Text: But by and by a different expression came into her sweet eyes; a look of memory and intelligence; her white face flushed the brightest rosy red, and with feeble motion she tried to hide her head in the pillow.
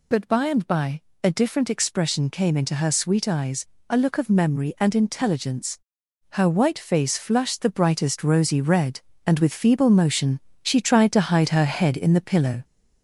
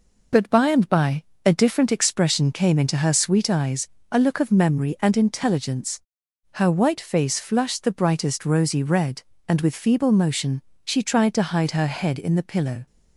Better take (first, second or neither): second